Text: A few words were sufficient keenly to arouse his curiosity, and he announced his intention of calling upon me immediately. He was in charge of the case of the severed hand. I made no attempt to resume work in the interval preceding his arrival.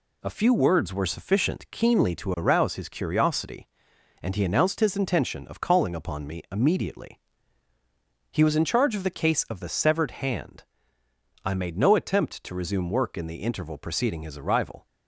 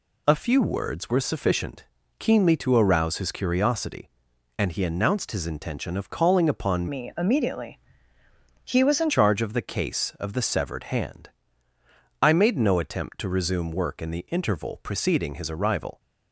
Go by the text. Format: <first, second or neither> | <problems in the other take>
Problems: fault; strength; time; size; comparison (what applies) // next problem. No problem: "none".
first | pauses between "sufficient" and "keenly"; slight; at 1.8 s; 0.32 s long // changes voice from "me" to "in"; from 6.8 to 9.1 s; 2.3 s long